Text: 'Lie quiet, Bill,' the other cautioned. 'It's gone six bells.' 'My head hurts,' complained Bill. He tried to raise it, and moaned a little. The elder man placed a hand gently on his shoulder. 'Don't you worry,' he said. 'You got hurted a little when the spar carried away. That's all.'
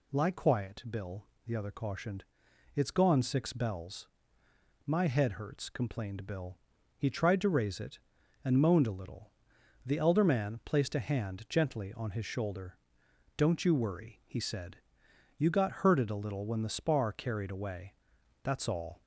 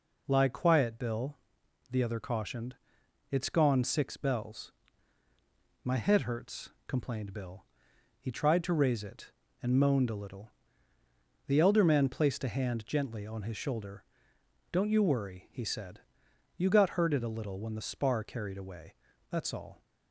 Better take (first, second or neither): neither